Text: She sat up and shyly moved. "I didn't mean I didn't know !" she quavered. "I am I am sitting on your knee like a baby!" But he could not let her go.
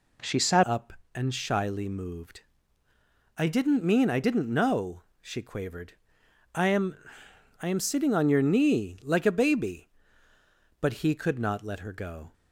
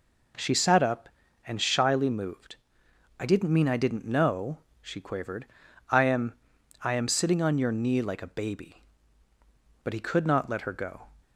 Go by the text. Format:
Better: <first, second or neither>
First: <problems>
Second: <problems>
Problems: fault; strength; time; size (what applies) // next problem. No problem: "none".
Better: second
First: changes voice at "up"; from 0.6 s on; 11.7 s long // pauses between "am" and "I"; noticeable; at 6.9 s; 0.68 s long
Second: pauses between "am" and "I"; noticeable; at 6.3 s; 0.48 s long